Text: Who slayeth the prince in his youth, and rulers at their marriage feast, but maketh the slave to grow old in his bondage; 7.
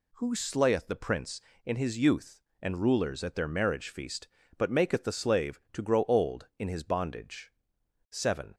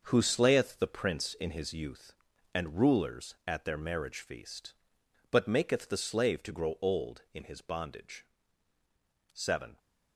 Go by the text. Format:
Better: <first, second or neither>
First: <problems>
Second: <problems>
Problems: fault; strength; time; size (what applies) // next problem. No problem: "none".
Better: first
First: none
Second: gets quieter; strong; throughout; 9 dB